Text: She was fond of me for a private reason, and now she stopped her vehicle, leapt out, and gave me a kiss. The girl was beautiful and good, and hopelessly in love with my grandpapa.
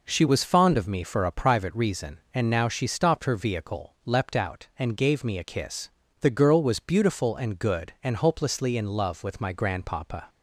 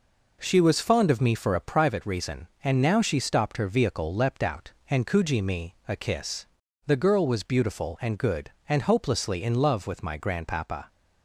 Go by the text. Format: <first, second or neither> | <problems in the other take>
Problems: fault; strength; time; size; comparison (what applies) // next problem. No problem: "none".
first | says "kuji" for "gave"; at 5.0 s